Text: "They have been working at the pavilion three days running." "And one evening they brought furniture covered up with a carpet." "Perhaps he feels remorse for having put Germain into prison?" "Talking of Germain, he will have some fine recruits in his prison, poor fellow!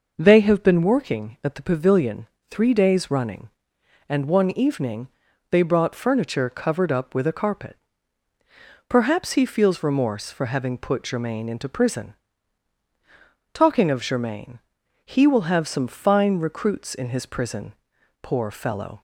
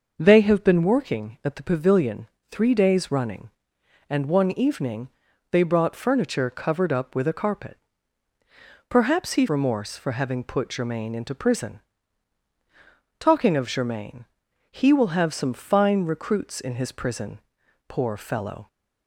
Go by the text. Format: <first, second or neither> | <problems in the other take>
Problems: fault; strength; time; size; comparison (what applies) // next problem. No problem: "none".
first | pauses between "pavilion" and "three"; slight; at 2.2 s; 0.22 s long; slight in the first // pauses between "evening" and "they"; at 5.0 s; 0.40 s long; also in the first // skips "feels"; at 9.4 s